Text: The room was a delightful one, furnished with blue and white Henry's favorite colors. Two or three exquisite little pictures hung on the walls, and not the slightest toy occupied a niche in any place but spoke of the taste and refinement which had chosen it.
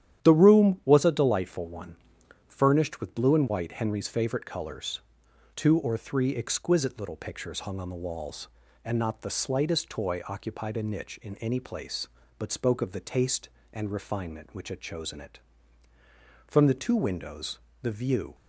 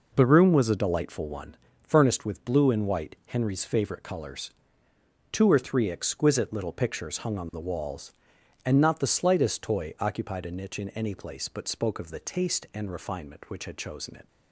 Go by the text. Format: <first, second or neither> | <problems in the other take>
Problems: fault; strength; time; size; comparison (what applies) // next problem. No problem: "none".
second | starts louder than the rest; strong; until 1.2 s; 10.5 dB // goes on to say "From the two windows the view"; strong; from 16.4 s on; 1.8 s long